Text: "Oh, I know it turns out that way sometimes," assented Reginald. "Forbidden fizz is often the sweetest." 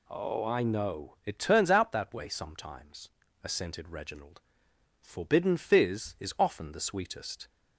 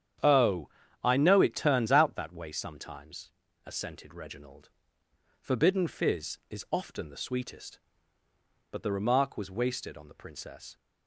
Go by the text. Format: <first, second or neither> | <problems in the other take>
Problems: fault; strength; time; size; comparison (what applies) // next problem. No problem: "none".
first | starts louder than the rest; strong; until 1.5 s; 9 dB // goes on to say "But the remark was wasted on the Princess"; strong; from 8.6 s on; 2.0 s long